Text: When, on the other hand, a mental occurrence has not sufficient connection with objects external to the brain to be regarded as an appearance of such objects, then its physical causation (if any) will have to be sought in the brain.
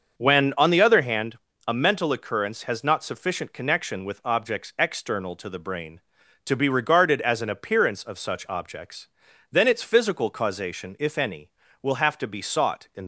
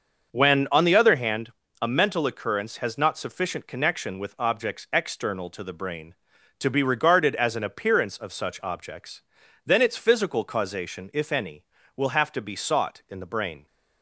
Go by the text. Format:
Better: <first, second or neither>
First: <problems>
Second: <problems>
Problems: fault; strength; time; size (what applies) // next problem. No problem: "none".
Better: second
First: starts louder than the rest; until 1.2 s; 6.5 dB // stops before "the brain"; at 13.0 s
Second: starts louder than the rest; until 1.3 s; 6.5 dB